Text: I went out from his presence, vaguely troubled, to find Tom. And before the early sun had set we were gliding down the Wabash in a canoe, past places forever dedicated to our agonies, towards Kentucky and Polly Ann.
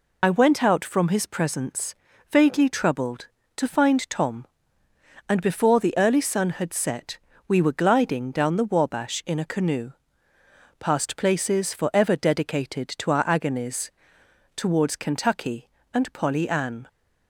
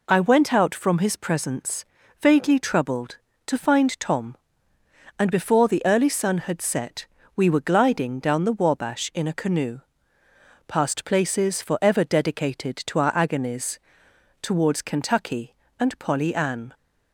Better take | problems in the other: second | loses the start of "I"; at 0.2 s; 55 ms // pauses between "set" and "we"; slight; at 7.1 s; 0.30 s long; slight in the second

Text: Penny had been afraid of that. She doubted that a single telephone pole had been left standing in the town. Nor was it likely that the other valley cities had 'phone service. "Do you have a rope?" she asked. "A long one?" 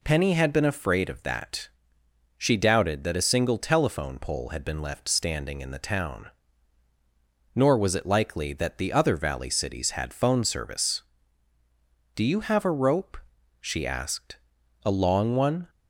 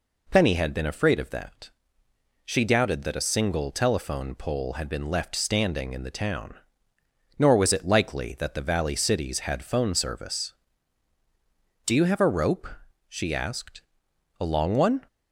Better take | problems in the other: first | skips "other"; at 8.6 s

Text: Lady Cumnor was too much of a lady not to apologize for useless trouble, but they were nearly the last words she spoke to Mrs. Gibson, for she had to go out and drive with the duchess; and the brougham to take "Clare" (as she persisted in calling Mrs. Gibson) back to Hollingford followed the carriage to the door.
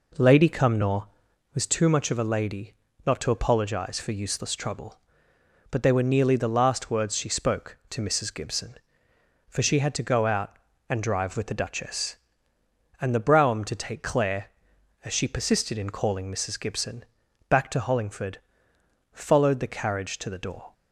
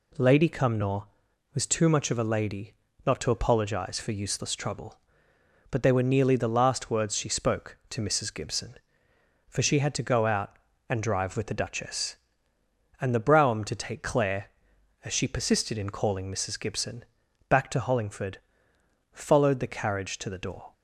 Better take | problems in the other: second | starts louder than the rest; noticeable; until 1.6 s; 4 dB // pauses between "lady" and "not"; slight; at 2.7 s; 0.32 s long; slight in the second // pauses between "Hollingford" and "followed"; noticeable; at 18.3 s; 0.76 s long; noticeable in the second

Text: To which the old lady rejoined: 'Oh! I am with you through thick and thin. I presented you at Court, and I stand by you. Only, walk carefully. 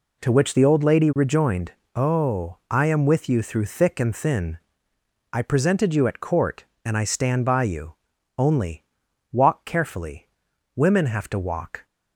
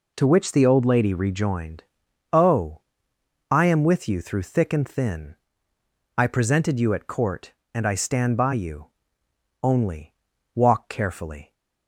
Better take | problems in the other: second | goes on to say "Women have to walk"; noticeable; from 10.7 s on; 1.1 s long

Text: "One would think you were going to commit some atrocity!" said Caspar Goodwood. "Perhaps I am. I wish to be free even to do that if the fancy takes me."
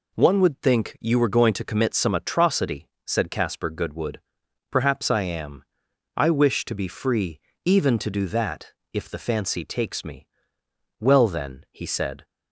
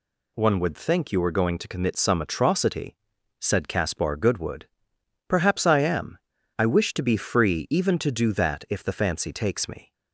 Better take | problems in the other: second | pauses between "free" and "even"; slight; at 7.3 s; 0.28 s long // pauses between "that" and "if"; slight; at 8.7 s; 0.22 s long // goes on to say "Well then he said"; noticeable; from 10.9 s on; 1.2 s long

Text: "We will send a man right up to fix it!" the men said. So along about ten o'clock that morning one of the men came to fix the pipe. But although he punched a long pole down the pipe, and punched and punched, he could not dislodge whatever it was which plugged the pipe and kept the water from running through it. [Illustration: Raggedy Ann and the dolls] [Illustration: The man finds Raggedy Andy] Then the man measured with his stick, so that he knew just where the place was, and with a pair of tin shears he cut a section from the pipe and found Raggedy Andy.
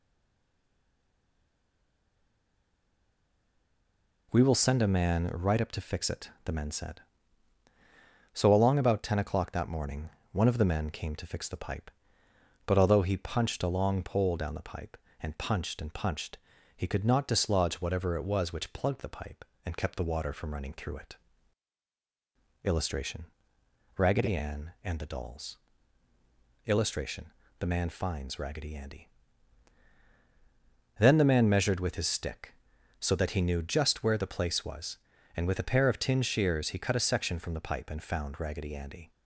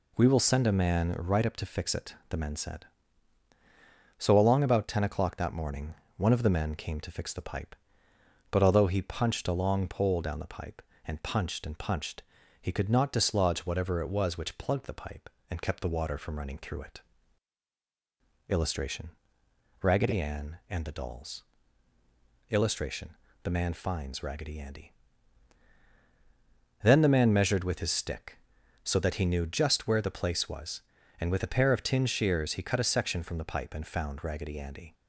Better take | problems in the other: second | stays silent before the first word; strong; until 4.3 s; 4.3 s long // pauses between "morning" and "one"; slight; at 10.1 s; 0.22 s long; slight in the second // pauses between "dolls" and "Illustration"; at 25.5 s; 1.1 s long; also in the second // pauses between "Andy" and "Then"; strong; at 29.0 s; 1.9 s long; strong in the second

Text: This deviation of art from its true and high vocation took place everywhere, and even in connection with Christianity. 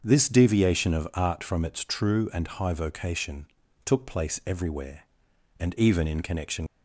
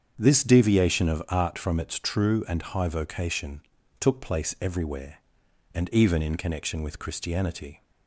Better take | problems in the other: second | starts louder than the rest; until 1.0 s; 6.5 dB; strong in the second // pauses between "vocation" and "took"; at 3.4 s; 0.40 s long; also in the second // stops before "with Christianity"; at 6.6 s

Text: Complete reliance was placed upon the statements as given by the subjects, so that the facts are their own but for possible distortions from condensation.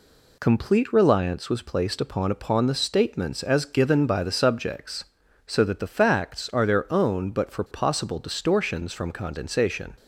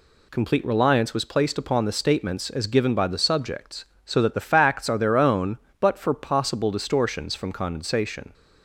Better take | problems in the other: second | says "upon" twice; at 2.3 s

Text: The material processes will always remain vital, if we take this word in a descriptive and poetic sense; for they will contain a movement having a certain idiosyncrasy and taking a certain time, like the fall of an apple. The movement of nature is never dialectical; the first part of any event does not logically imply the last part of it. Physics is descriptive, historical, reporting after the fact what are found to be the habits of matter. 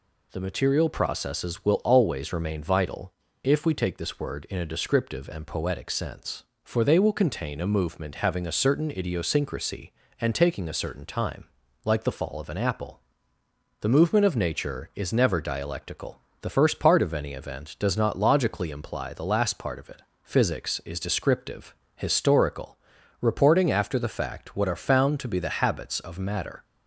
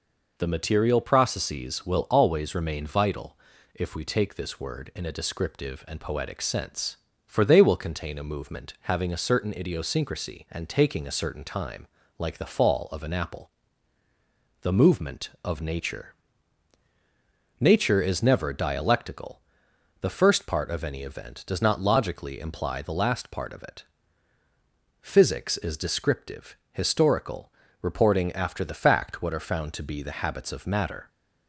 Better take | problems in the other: first | says "nature" twice; at 17.6 s

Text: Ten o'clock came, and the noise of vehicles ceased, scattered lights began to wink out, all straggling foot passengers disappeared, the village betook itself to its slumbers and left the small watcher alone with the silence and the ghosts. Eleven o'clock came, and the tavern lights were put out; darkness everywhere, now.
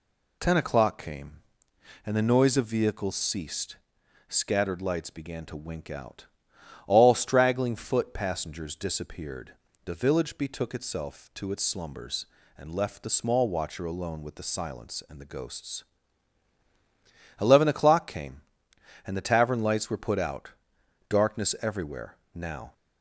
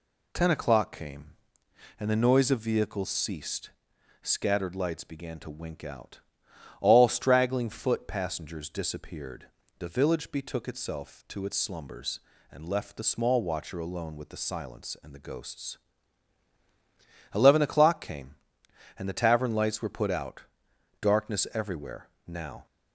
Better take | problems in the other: neither | none

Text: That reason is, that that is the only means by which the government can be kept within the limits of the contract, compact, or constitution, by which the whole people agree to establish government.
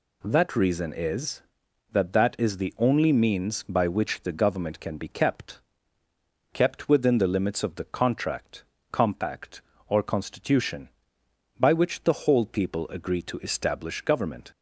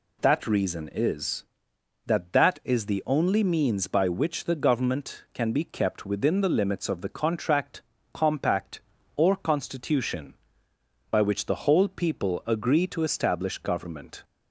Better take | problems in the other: second | says "kept" twice; at 6.5 s

